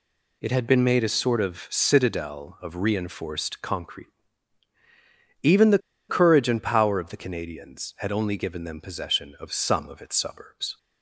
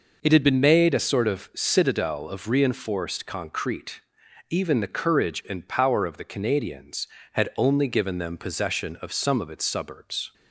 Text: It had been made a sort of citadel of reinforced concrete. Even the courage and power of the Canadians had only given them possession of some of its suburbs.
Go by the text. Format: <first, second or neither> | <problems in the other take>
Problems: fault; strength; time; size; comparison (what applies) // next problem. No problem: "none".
second | pauses between "the" and "courage"; slight; at 5.7 s; 0.29 s long